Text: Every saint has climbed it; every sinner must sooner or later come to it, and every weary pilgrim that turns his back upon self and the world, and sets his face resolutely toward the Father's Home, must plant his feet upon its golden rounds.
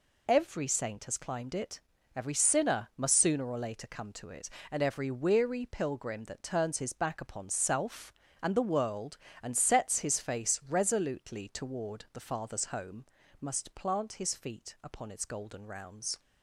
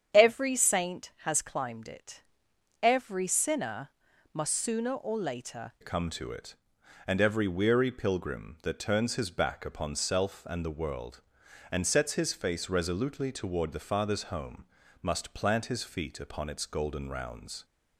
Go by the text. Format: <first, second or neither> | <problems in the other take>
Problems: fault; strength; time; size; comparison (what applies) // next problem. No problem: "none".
first | starts louder than the rest; strong; until 1.2 s; 8.5 dB // pauses between "sinner" and "must"; at 3.9 s; 0.42 s long // changes voice at "come"; from 5.8 s on; 11.8 s long